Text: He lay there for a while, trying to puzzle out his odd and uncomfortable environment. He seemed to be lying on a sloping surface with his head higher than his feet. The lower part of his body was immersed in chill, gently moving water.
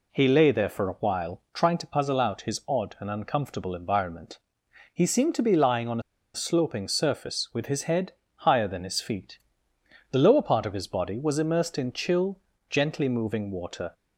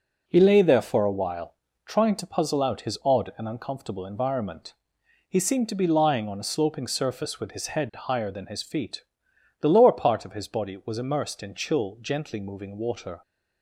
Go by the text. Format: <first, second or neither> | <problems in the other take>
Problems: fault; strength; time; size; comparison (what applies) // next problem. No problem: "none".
second | pauses between "on" and "a"; slight; at 5.9 s; 0.34 s long // pauses between "head" and "higher"; slight; at 8.1 s; 0.24 s long